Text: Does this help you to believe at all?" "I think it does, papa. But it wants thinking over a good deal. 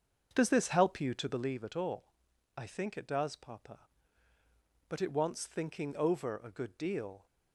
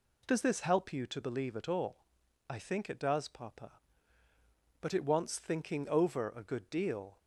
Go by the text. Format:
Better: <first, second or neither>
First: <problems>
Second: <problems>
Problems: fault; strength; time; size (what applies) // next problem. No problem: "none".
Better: second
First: starts louder than the rest; until 1.6 s; 6.5 dB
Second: none